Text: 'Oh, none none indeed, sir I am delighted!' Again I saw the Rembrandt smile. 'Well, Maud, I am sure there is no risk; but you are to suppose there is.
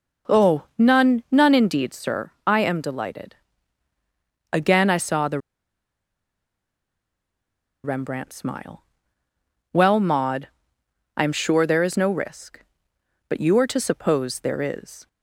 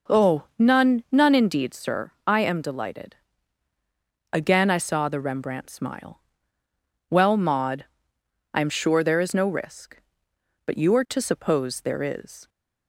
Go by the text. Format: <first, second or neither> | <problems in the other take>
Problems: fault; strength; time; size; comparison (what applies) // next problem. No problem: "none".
second | pauses between "the" and "Rembrandt"; strong; at 5.3 s; 2.4 s long